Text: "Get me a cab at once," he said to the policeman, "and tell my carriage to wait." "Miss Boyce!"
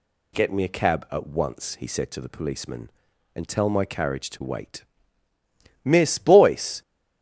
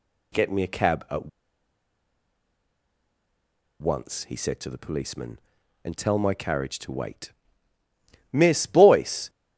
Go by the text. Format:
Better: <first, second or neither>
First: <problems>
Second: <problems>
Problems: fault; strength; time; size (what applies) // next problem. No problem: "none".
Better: first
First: none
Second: pauses between "at" and "once"; strong; at 1.2 s; 2.5 s long